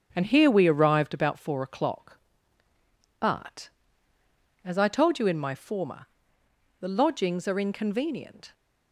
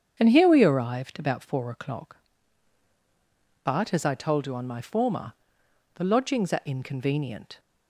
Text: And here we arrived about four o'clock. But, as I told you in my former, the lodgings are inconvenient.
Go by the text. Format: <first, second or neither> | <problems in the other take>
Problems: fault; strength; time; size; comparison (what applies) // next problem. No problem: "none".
first | starts louder than the rest; strong; until 1.1 s; 7.5 dB; strong in the first // says "on" for "in"; at 4.5 s